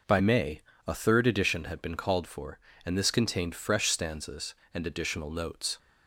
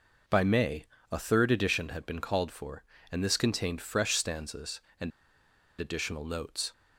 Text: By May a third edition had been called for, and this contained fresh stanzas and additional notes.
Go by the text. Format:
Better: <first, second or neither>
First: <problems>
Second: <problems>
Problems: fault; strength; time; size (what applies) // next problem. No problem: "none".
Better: first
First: pauses between "May" and "a"; slight; at 0.6 s; 0.26 s long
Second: pauses between "May" and "a"; slight; at 0.8 s; 0.26 s long // pauses between "and" and "additional"; noticeable; at 5.1 s; 0.69 s long